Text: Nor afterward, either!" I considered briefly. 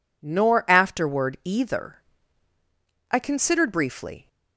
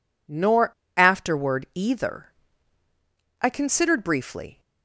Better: first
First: none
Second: pauses between "Nor" and "afterward"; slight; at 0.7 s; 0.26 s long

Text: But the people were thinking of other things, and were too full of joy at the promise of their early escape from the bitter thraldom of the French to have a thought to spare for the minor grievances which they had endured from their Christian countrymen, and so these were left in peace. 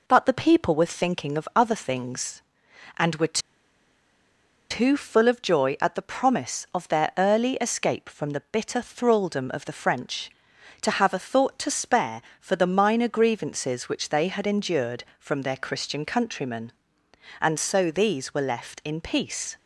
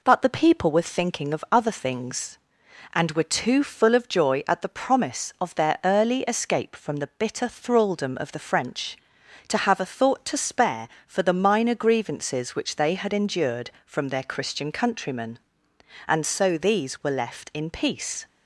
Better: second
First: pauses between "were" and "too"; strong; at 3.3 s; 1.3 s long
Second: none

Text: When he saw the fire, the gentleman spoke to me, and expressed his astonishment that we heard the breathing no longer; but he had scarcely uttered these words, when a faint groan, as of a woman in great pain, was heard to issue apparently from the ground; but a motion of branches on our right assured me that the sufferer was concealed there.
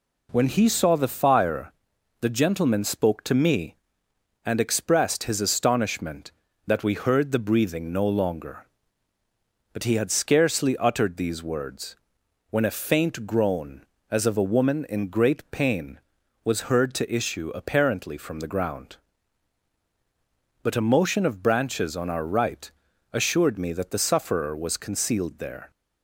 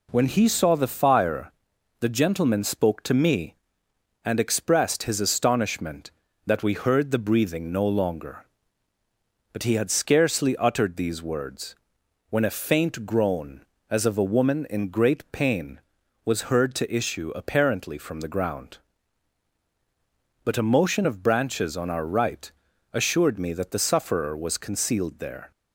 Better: neither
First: pauses between "right" and "assured"; at 22.7 s; 0.44 s long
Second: pauses between "right" and "assured"; at 22.5 s; 0.44 s long

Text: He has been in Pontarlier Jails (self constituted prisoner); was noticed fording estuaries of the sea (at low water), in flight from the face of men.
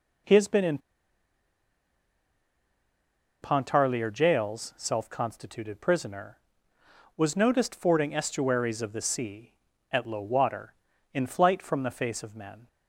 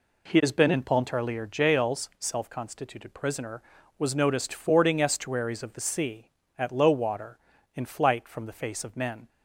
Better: second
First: pauses between "in" and "Pontarlier"; strong; at 0.7 s; 2.6 s long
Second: none

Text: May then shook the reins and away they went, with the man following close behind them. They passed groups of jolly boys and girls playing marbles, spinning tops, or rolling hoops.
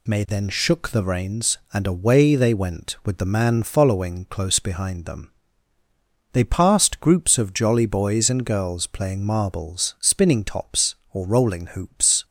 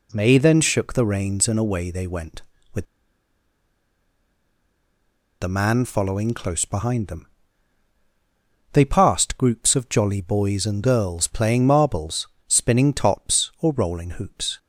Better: first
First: none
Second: pauses between "with" and "the"; strong; at 2.8 s; 2.5 s long

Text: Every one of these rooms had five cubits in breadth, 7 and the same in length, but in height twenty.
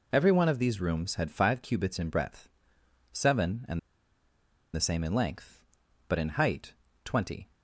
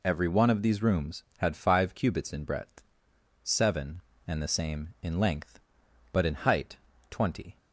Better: second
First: pauses between "and" and "the"; noticeable; at 3.7 s; 0.95 s long // pauses between "height" and "twenty"; slight; at 6.7 s; 0.30 s long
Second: pauses between "height" and "twenty"; slight; at 6.7 s; 0.32 s long

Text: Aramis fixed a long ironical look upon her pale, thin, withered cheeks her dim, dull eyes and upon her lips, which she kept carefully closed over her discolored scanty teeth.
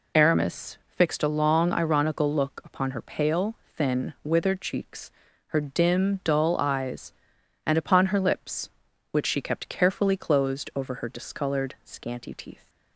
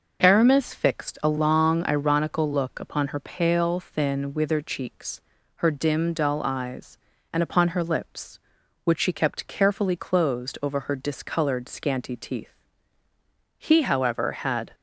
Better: first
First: pauses between "cheeks" and "her"; slight; at 5.1 s; 0.36 s long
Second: pauses between "cheeks" and "her"; slight; at 5.1 s; 0.36 s long // goes on to say "He however had"; noticeable; from 13.5 s on; 1.1 s long

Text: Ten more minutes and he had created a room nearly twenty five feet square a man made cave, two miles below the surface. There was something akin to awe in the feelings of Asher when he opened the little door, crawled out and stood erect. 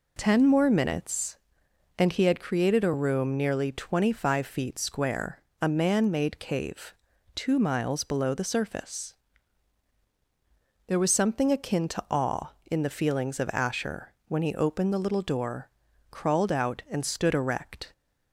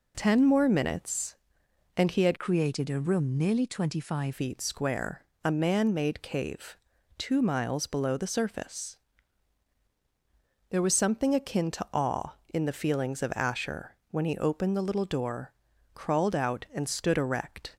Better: first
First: pauses between "square" and "a"; slight; at 5.4 s; 0.18 s long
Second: changes voice from "created" to "five"; from 2.3 to 4.3 s; 2.0 s long // pauses between "square" and "a"; slight; at 5.2 s; 0.18 s long

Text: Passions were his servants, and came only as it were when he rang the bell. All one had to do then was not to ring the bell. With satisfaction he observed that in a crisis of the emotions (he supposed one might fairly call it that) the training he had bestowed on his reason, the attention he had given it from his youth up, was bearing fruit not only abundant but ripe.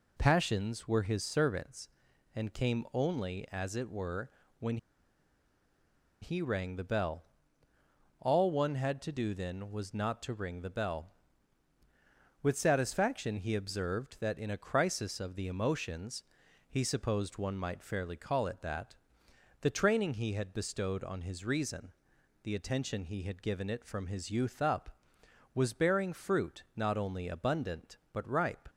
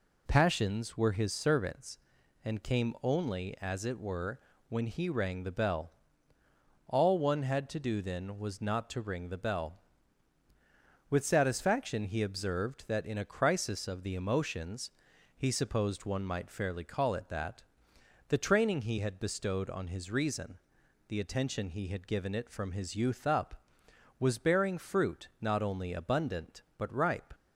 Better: second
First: pauses between "were" and "when"; slight; at 4.2 s; 0.30 s long // pauses between "when" and "he"; strong; at 4.7 s; 1.4 s long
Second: pauses between "were" and "when"; slight; at 4.3 s; 0.30 s long

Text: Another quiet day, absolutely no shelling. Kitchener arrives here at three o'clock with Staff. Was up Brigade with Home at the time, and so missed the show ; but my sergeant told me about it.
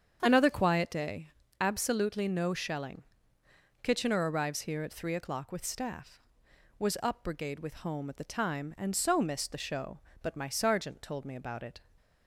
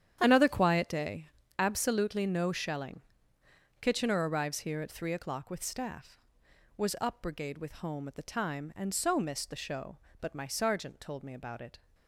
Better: first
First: starts louder than the rest; strong; until 1.2 s; 7.5 dB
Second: gets quieter; strong; throughout; 12.5 dB // starts louder than the rest; strong; until 1.2 s; 9.5 dB

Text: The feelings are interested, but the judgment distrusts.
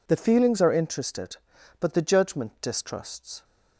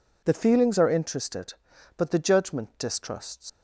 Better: first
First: none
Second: leaves "distrusts" unfinished; at 3.4 s; 105 ms

